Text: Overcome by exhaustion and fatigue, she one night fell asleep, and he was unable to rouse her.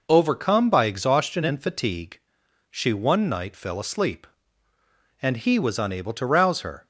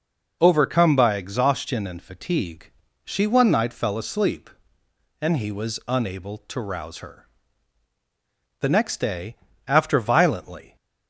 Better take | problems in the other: first | goes on to say "The next day after violently"; strong; from 8.5 s on; 2.1 s long

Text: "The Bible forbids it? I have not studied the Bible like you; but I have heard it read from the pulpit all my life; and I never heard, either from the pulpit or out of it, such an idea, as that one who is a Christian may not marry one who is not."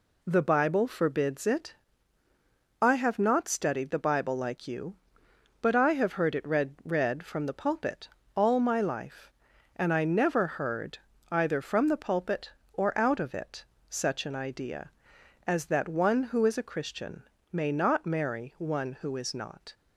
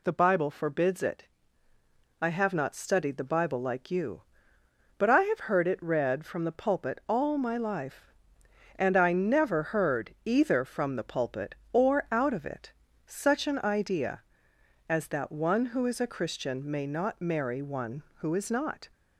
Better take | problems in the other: second | says "read" twice; at 6.8 s // pauses between "pulpit" and "all"; slight; at 8.0 s; 0.28 s long // pauses between "Christian" and "may"; slight; at 17.2 s; 0.28 s long

